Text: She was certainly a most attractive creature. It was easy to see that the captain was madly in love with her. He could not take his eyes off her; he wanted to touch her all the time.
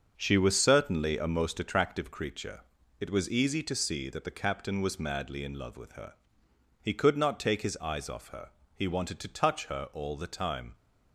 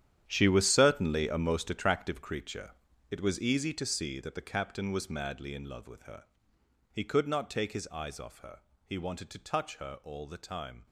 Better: first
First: starts louder than the rest; until 1.1 s; 6.5 dB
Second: gets quieter; strong; throughout; 14.5 dB // starts louder than the rest; strong; until 1.2 s; 10 dB

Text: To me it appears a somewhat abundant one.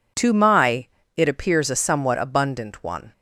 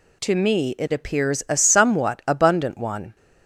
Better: second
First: says "my" for "me"; at 0.3 s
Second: none

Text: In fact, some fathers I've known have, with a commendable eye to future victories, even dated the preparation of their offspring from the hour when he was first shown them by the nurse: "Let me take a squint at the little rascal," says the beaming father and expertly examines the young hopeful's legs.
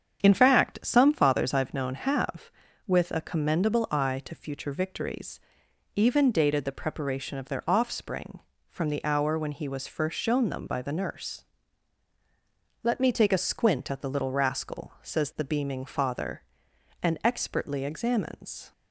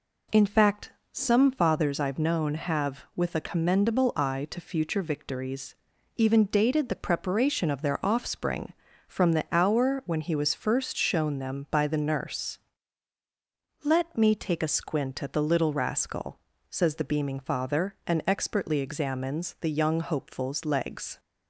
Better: second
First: starts louder than the rest; strong; until 1.2 s; 8 dB // stops before "the young hopeful's legs"; at 18.7 s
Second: none

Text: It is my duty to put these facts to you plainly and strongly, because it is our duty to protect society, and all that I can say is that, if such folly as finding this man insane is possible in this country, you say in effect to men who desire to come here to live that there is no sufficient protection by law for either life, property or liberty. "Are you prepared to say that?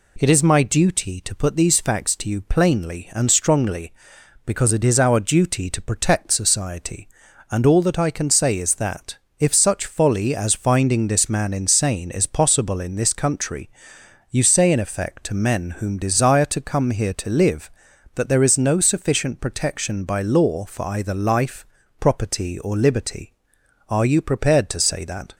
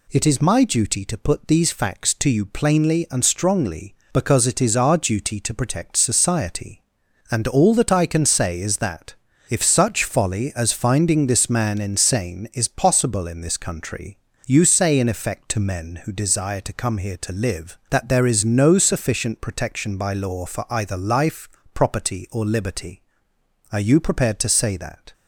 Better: second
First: says "whom" for "who"; at 15.8 s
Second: none

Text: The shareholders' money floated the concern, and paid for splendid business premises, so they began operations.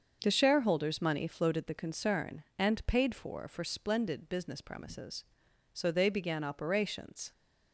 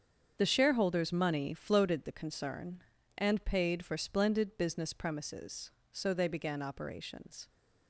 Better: second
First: starts louder than the rest; until 1.2 s; 6.5 dB // says "for" twice; at 3.4 s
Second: starts louder than the rest; strong; until 1.4 s; 7.5 dB

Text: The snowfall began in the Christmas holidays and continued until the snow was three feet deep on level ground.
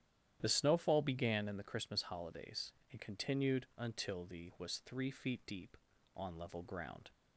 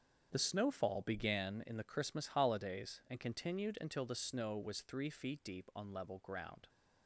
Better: second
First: starts louder than the rest; strong; until 1.4 s; 11 dB // skips "snow"; at 4.5 s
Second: starts louder than the rest; strong; until 1.3 s; 7.5 dB

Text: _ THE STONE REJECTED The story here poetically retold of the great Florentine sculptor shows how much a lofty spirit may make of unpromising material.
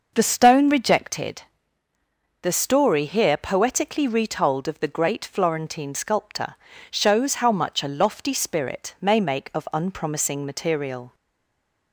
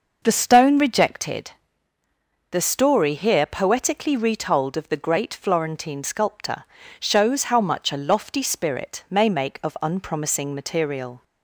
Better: second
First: pauses between "REJECTED" and "The"; at 1.4 s; 1.0 s long // pauses between "sculptor" and "shows"; at 6.5 s; 0.38 s long // stays silent after the last word; slight; from 11.1 s on; 0.8 s long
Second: pauses between "REJECTED" and "The"; at 1.5 s; 1.0 s long // pauses between "sculptor" and "shows"; at 6.6 s; 0.38 s long

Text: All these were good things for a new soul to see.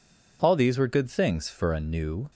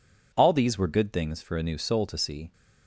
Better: second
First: stops before "soul to see"; at 2.3 s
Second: none

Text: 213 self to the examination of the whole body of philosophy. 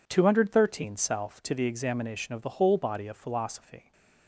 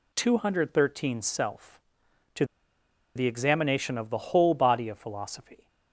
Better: first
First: none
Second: pauses between "to" and "the"; noticeable; at 2.4 s; 0.71 s long

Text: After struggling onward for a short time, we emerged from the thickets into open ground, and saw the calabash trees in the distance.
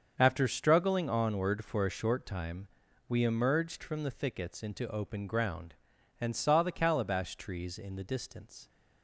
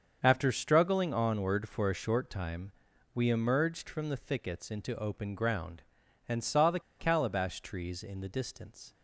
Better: first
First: starts louder than the rest; until 1.1 s; 7 dB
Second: starts louder than the rest; until 1.2 s; 7 dB // pauses between "the" and "calabash"; slight; at 6.7 s; 0.19 s long

